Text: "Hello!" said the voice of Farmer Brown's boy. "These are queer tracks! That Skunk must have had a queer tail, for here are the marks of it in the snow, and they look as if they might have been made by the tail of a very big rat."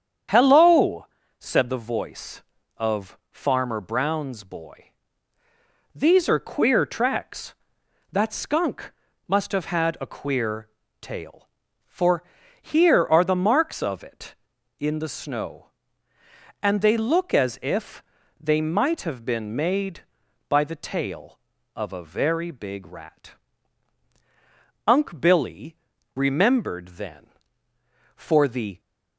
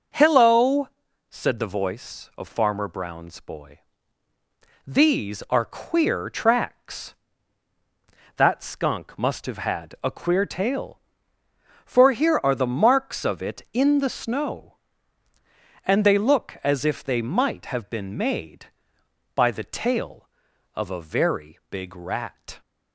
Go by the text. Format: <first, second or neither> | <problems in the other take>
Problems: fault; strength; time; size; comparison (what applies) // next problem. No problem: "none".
second | starts louder than the rest; strong; until 1.6 s; 8 dB; also in the second // pauses between "Skunk" and "must"; slight; at 8.9 s; 0.34 s long // pauses between "queer" and "tail"; slight; at 10.6 s; 0.32 s long // pauses between "for" and "here"; at 12.2 s; 0.40 s long // pauses between "if" and "they"; slight; at 18.0 s; 0.36 s long // goes on to say "Unc Billy remembered then for the"; strong; from 24.8 s on; 3.9 s long